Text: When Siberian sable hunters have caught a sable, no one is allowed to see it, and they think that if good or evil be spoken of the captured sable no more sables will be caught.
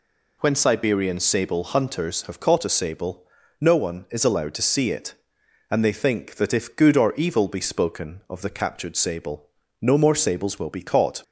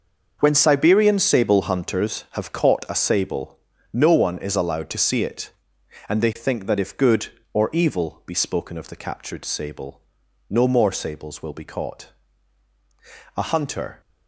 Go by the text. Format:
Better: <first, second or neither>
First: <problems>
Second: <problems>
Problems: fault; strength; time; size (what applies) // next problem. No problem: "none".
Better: first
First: pauses between "sable" and "no"; slight; at 9.4 s; 0.34 s long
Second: starts louder than the rest; until 1.4 s; 6 dB // pauses between "sable" and "no"; noticeable; at 10.0 s; 0.48 s long // goes on to say "A hunter"; noticeable; from 13.3 s on; 0.64 s long